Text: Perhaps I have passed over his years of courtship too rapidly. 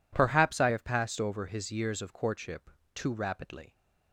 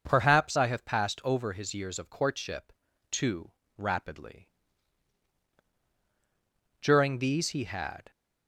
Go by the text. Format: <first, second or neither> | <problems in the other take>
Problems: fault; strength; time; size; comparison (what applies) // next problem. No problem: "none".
first | pauses between "courtship" and "too"; at 2.7 s; 0.38 s long; slight in the first // pauses between "too" and "rapidly"; slight; at 3.5 s; 0.26 s long // goes on to say "During these he had"; noticeable; from 6.8 s on; 1.3 s long